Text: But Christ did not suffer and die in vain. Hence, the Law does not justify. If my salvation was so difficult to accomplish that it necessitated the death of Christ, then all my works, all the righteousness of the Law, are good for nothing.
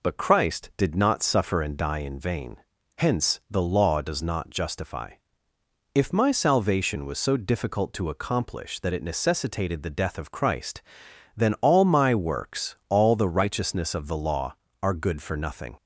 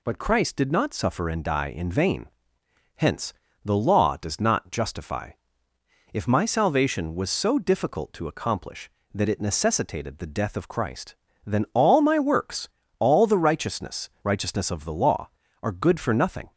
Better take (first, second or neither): first